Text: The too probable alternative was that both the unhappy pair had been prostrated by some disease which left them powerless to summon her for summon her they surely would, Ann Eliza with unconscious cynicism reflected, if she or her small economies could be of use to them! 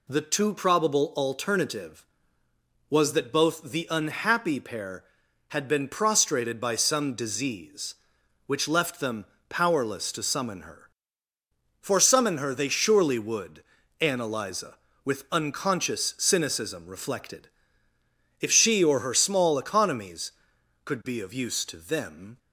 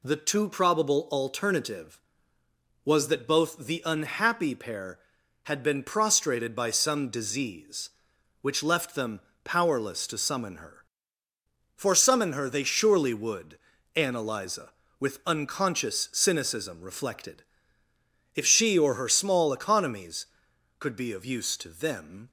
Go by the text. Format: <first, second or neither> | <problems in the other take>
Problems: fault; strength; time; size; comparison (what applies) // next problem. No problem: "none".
neither | pauses between "them" and "powerless"; slight; the same in both